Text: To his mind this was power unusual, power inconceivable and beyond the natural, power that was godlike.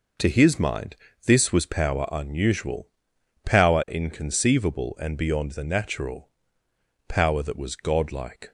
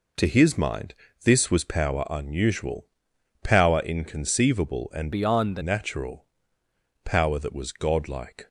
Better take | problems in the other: first | pauses between "mind" and "this"; slight; at 0.9 s; 0.30 s long; slight in the first // changes voice from "beyond" to "the"; from 5.1 to 5.6 s; 0.5 s long

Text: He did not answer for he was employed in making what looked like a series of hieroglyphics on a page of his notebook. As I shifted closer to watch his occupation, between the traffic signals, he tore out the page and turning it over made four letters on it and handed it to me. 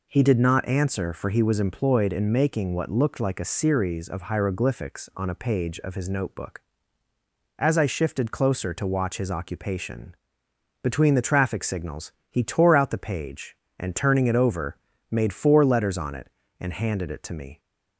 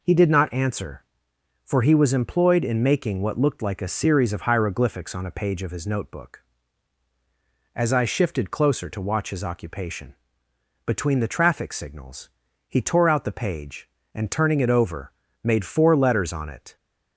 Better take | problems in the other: first | pauses between "over" and "made"; slight; at 15.1 s; 0.28 s long; slight in the first // stops before "and handed it to me"; at 16.7 s

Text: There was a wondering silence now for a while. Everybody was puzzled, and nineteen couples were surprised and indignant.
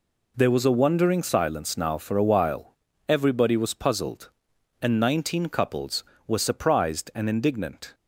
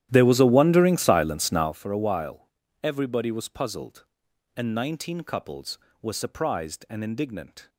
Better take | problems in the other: first | starts louder than the rest; strong; until 1.7 s; 12 dB

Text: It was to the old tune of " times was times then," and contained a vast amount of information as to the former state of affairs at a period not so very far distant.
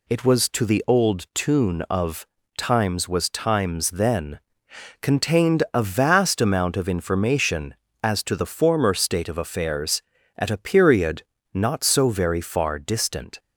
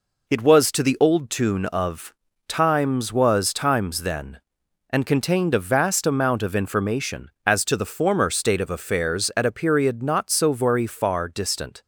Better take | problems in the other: second | skips "and"; at 4.6 s // pauses between "period" and "not"; slight; at 11.2 s; 0.32 s long

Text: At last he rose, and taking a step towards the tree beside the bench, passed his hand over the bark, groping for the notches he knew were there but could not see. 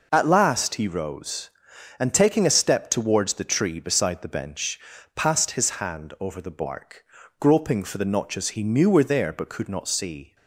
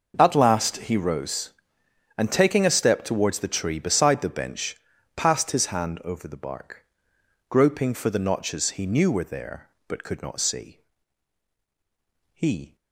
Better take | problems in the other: first | goes on to say "He"; slight; from 12.3 s on; 0.42 s long

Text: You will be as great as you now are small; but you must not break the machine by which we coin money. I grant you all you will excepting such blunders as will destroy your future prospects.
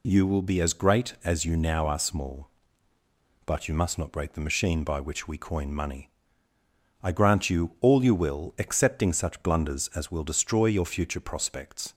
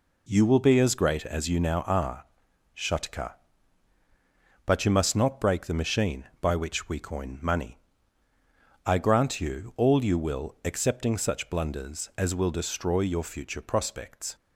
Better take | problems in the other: first | says "shatka" for "small"; at 2.7 s

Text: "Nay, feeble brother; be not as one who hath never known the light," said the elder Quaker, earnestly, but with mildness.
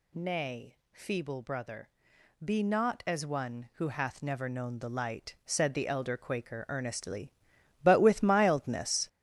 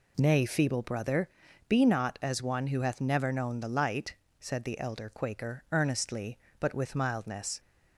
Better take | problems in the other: second | gets louder; strong; throughout; 8.5 dB

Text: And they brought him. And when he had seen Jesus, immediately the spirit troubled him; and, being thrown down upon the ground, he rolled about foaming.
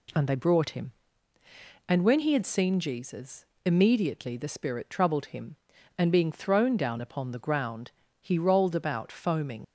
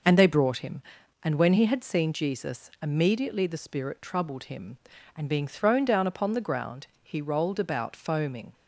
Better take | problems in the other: second | leaves "foaming" unfinished; at 9.6 s; 65 ms

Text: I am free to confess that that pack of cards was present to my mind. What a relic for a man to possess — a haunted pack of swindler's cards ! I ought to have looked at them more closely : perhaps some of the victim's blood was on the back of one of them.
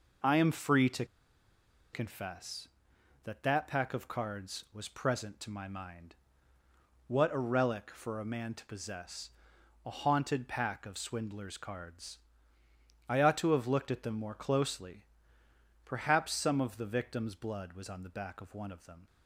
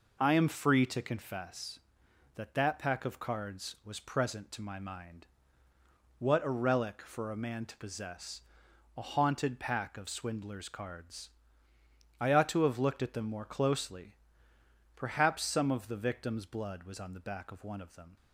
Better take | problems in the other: second | pauses between "to" and "confess"; noticeable; at 1.0 s; 0.87 s long

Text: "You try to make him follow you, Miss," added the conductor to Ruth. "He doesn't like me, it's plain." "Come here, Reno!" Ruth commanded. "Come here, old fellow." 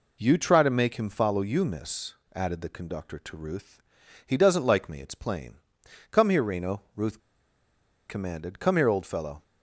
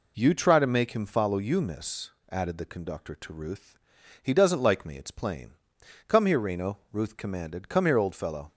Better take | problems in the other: second | pauses between "Ruth" and "commanded"; noticeable; at 7.2 s; 0.88 s long

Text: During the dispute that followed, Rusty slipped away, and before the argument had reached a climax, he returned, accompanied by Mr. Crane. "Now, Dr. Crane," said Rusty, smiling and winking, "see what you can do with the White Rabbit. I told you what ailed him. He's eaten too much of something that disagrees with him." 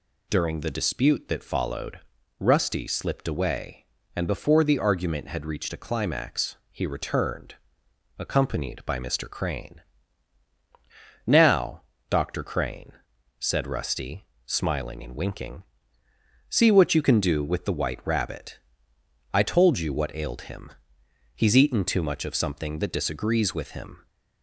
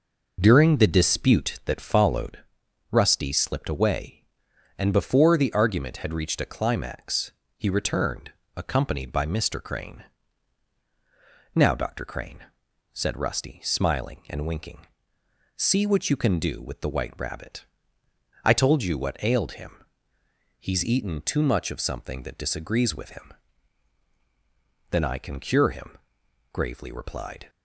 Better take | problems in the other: first | goes on to say "Then I can cure him gravely replied"; strong; from 24.9 s on; 2.5 s long

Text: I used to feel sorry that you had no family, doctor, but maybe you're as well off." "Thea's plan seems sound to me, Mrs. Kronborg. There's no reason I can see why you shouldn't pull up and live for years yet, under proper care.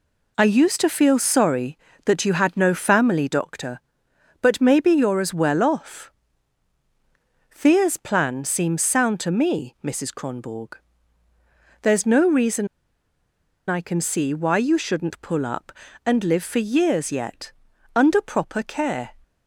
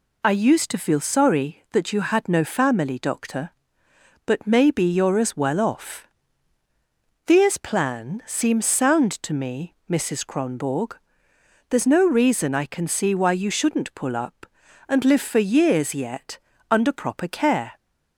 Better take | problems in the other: second | pauses between "reason" and "I"; at 12.6 s; 1.0 s long

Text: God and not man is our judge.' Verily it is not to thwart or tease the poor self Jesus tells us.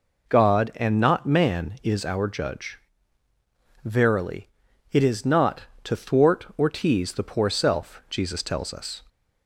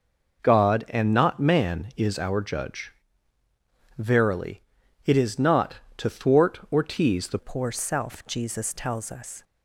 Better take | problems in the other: first | pauses between "Verily" and "it"; at 4.6 s; 0.44 s long; also in the first // changes voice at "poor"; from 7.3 s on; 2.1 s long

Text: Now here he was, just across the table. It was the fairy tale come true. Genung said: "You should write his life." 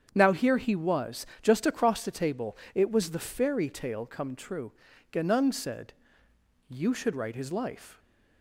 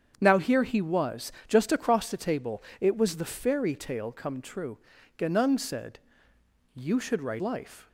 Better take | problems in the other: first | starts louder than the rest; strong; until 1.2 s; 7.5 dB; strong in the first // skips "his"; at 7.4 s

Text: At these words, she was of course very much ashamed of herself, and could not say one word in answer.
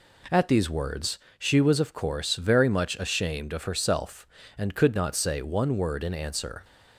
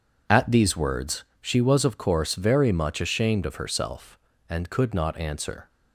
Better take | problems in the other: first | skips "say one word in"; at 5.1 s

